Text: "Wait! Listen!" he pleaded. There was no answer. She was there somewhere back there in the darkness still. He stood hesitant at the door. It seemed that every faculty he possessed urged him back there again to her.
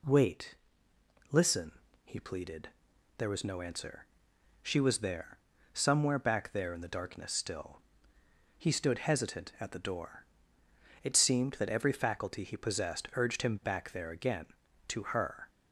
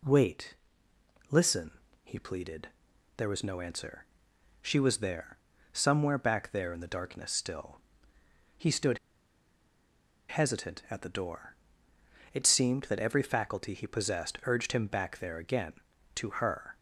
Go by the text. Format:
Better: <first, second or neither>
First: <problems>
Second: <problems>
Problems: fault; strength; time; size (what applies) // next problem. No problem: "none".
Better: first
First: pauses between "there" and "somewhere"; slight; at 5.3 s; 0.34 s long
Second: pauses between "there" and "somewhere"; slight; at 5.3 s; 0.34 s long // pauses between "stood" and "hesitant"; strong; at 8.9 s; 1.3 s long